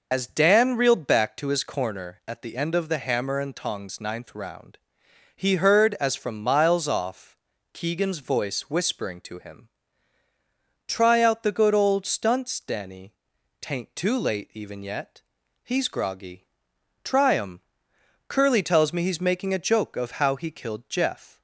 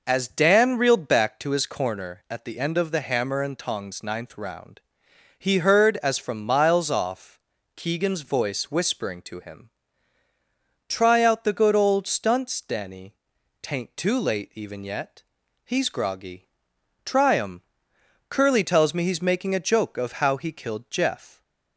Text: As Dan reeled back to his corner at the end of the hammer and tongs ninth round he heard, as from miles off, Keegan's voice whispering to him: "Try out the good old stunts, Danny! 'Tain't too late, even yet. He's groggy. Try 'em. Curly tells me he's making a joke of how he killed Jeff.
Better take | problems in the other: second | loses the start of "As"; at 0.1 s; 65 ms // pauses between "round" and "he"; noticeable; at 4.7 s; 0.58 s long; noticeable in the second

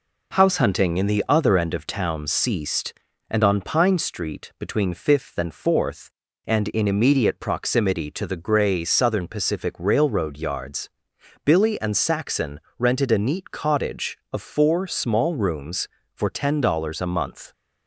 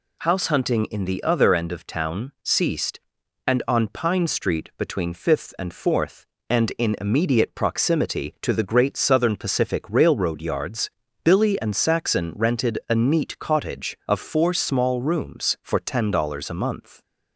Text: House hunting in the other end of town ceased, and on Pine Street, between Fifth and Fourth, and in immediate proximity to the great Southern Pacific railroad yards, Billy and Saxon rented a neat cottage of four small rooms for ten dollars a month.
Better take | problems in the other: second | says "grey" for "great"; at 8.3 s // pauses between "Saxon" and "rented"; slight; at 12.5 s; 0.18 s long

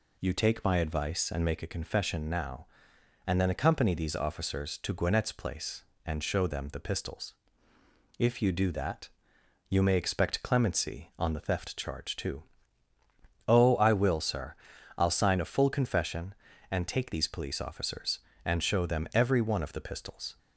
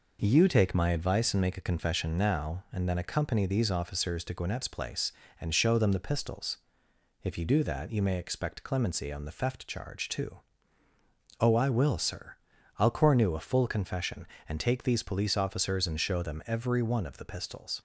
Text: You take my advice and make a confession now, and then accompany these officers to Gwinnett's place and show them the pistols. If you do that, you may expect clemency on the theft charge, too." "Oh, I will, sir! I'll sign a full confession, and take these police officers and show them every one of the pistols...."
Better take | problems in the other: first | says "cornu" for "sign"; at 12.9 s

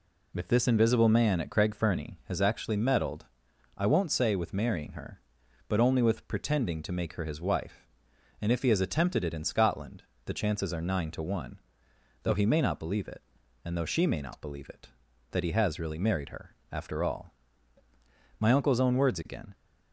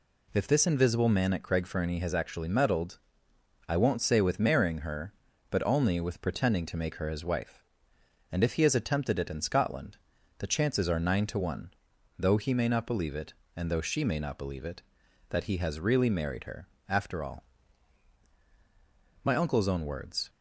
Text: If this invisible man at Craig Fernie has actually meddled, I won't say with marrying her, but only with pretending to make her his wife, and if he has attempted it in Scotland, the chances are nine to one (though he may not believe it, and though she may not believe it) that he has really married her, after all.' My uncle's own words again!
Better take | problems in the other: first | stops before "again"; at 20.2 s

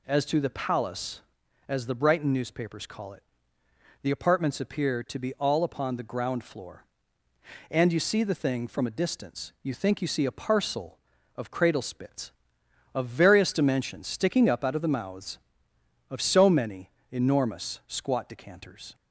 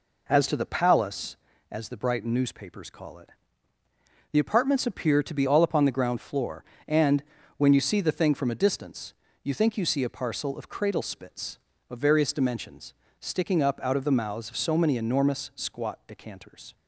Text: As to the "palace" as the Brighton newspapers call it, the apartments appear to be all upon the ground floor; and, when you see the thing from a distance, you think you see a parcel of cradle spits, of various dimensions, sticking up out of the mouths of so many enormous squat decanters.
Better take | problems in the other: second | skips "when"; at 7.9 s // pauses between "many" and "enormous"; slight; at 16.9 s; 0.20 s long

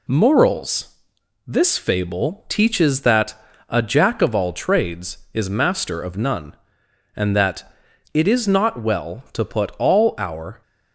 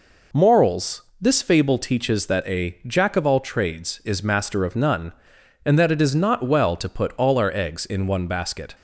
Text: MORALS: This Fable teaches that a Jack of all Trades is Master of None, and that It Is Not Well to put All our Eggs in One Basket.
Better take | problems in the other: second | pauses between "that" and "a"; slight; at 3.3 s; 0.34 s long // pauses between "that" and "It"; at 7.6 s; 0.44 s long // stops before "Eggs in One Basket"; at 10.6 s

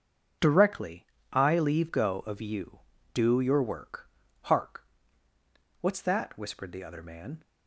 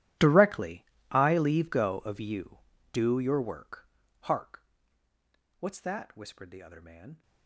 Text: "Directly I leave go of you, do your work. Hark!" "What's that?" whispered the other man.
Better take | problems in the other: first | gets quieter; strong; throughout; 22.5 dB // starts louder than the rest; strong; until 1.4 s; 13.5 dB; also in the first // pauses between "Directly" and "I"; slight; at 0.8 s; 0.28 s long; slight in the first

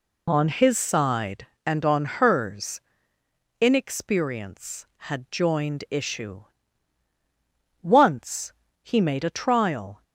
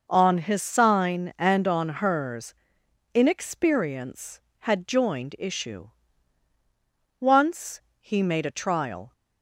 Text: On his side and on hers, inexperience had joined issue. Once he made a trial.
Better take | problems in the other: first | says "sign" for "side"; at 0.6 s // pauses between "Once" and "he"; slight; at 7.7 s; 0.20 s long; slight in the first

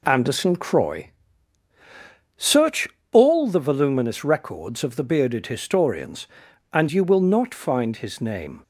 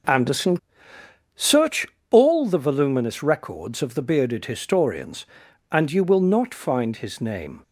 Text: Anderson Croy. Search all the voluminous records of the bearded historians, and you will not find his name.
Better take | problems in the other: first | skips "Croy"; at 0.9 s // pauses between "Search" and "all"; slight; at 1.8 s; 0.24 s long; slight in the first

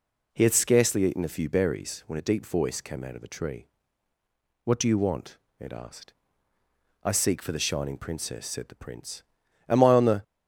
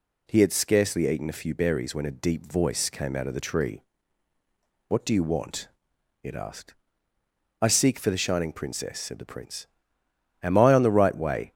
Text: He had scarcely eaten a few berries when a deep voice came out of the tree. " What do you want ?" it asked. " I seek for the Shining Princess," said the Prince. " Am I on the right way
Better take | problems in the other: second | starts louder than the rest; strong; until 1.3 s; 8 dB // stops before "right way"; at 10.2 s

